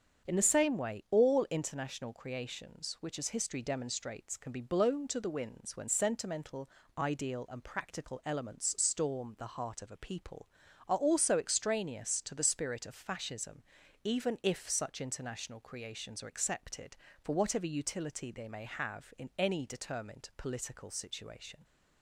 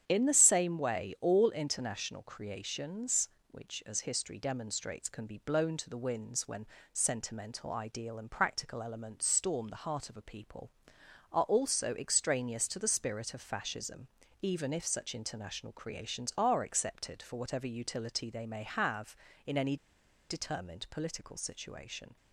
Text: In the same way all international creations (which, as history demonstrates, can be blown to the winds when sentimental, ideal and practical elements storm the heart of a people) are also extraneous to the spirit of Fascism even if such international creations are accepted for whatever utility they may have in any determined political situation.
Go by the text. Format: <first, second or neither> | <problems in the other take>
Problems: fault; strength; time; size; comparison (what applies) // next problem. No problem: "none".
first | starts louder than the rest; strong; until 1.0 s; 8.5 dB; strong in the first // pauses between "when" and "sentimental"; slight; at 6.6 s; 0.26 s long // pauses between "Fascism" and "even"; slight; at 14.0 s; 0.36 s long; also in the first // pauses between "any" and "determined"; noticeable; at 19.7 s; 0.53 s long